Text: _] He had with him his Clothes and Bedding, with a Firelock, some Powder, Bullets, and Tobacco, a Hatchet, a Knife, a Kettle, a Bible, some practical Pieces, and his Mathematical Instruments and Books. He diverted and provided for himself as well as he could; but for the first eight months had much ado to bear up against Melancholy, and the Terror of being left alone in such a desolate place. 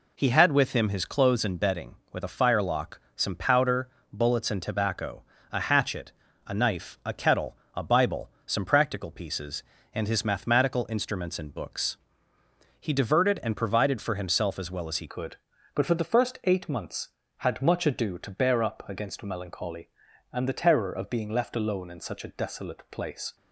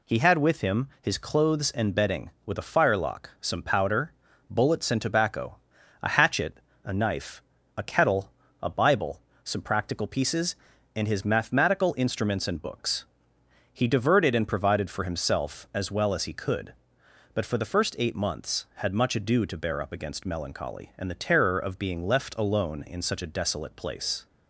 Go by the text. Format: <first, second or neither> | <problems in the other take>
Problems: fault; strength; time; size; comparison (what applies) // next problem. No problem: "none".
second | changes voice at "could"; from 15.0 s on; 8.3 s long